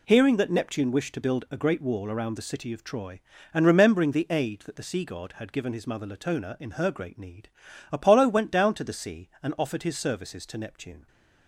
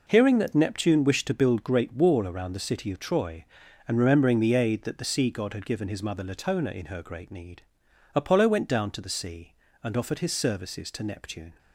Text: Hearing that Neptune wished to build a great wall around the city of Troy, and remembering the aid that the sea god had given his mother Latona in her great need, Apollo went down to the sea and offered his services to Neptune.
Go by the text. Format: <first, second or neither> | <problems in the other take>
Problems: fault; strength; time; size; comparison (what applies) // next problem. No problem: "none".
first | skips "a"; at 1.6 s